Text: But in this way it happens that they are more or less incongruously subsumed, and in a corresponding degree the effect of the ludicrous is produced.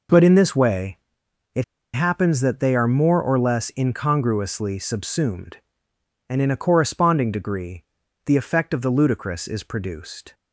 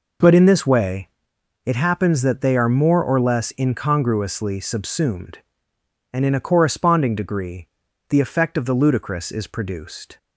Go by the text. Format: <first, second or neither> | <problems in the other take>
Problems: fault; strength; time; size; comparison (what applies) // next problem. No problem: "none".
second | pauses between "way" and "it"; noticeable; at 0.9 s; 0.58 s long; noticeable in the second // pauses between "it" and "happens"; slight; at 1.6 s; 0.29 s long // pauses between "degree" and "the"; at 7.8 s; 0.40 s long; also in the second